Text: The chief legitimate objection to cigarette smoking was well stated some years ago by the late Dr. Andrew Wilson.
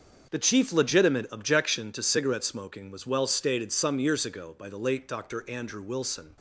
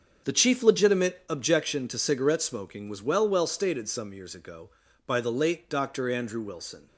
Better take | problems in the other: first | starts louder than the rest; until 1.3 s; 6.5 dB; also in the first // says "well" twice; at 3.2 s

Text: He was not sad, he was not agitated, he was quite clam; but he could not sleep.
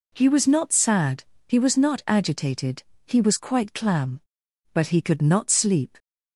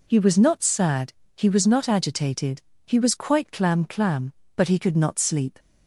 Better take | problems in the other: first | says "clam" twice; at 3.8 s

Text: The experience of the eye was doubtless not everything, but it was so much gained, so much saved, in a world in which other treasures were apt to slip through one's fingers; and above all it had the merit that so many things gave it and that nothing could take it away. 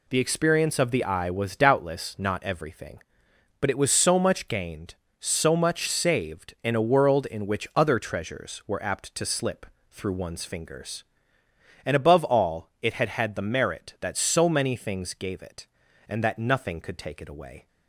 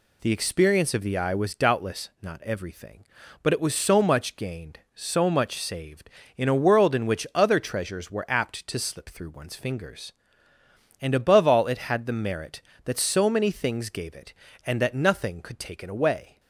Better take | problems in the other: second | pauses between "slip" and "through"; slight; at 9.6 s; 0.26 s long // says "had" twice; at 13.0 s

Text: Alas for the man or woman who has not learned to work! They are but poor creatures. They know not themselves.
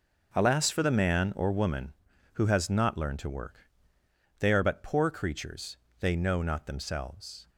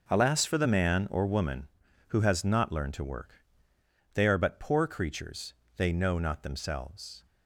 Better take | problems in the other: neither | none

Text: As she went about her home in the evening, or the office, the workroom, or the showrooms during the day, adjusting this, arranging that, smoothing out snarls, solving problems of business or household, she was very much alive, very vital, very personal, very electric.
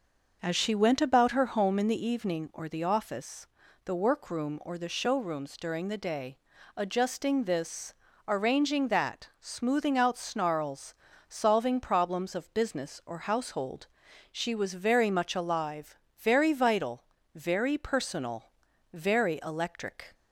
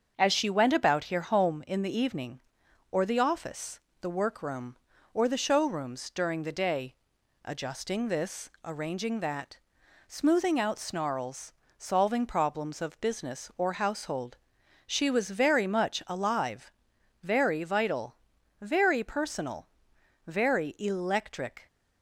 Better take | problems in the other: first | starts louder than the rest; until 1.1 s; 7 dB; noticeable in the first // says "here" for "her"; at 1.0 s

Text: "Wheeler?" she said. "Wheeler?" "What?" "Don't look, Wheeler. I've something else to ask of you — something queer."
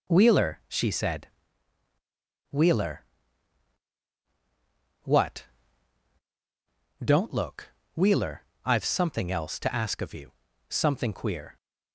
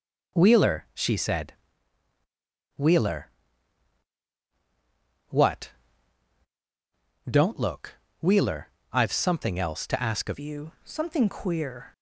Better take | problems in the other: first | changes voice at "you"; from 10.3 s on; 1.6 s long

